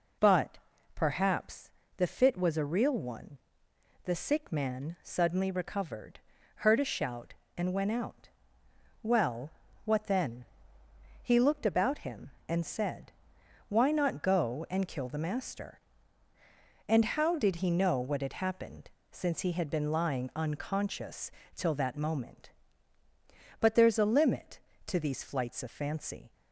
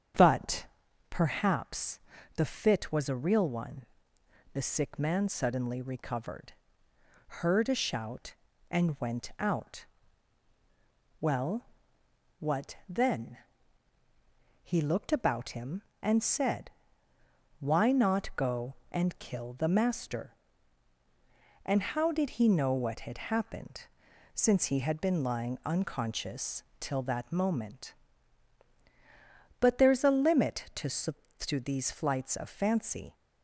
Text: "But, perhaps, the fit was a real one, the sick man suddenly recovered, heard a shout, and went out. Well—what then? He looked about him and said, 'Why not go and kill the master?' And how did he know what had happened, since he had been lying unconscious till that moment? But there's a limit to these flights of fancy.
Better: first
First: pauses between "unconscious" and "till"; slight; at 21.3 s; 0.24 s long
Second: starts louder than the rest; strong; until 1.6 s; 7.5 dB // pauses between "unconscious" and "till"; slight; at 26.6 s; 0.18 s long // says "to" twice; at 31.3 s

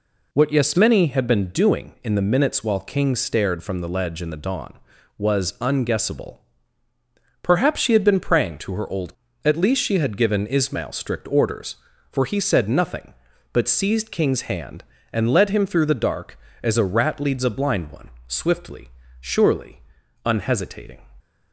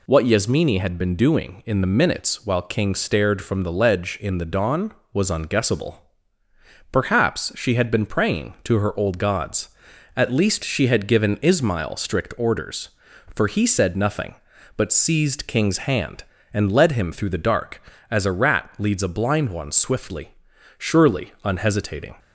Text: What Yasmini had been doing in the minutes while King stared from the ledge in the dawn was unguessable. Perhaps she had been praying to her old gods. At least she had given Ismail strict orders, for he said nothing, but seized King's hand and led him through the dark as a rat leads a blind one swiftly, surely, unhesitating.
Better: second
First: skips "gods"; at 9.2 s // pauses between "one" and "swiftly"; slight; at 18.0 s; 0.18 s long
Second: none

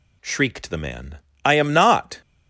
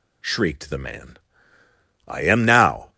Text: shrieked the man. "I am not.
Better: first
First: none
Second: says "now" for "not"; at 2.4 s

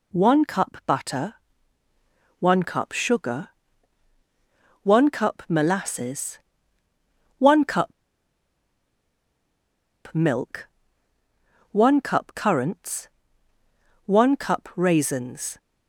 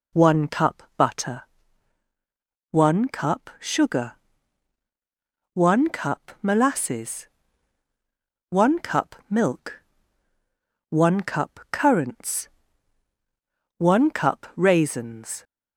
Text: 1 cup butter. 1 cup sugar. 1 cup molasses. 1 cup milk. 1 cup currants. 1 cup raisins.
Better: second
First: pauses between "cup" and "milk"; strong; at 7.9 s; 2.2 s long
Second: none

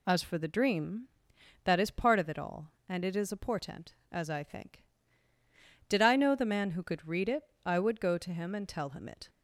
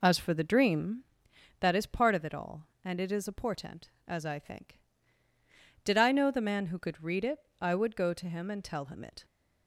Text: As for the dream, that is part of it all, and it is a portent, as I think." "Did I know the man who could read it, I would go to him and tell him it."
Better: first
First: none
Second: starts louder than the rest; until 1.2 s; 4 dB

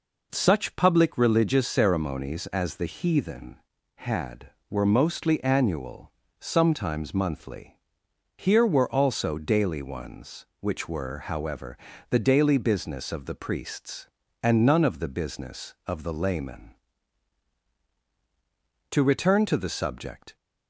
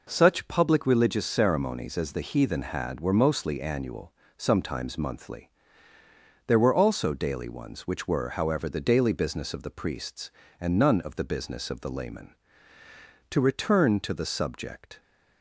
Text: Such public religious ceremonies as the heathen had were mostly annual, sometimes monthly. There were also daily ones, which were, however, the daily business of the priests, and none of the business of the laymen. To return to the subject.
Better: second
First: says "Here" for "There"; at 8.3 s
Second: none

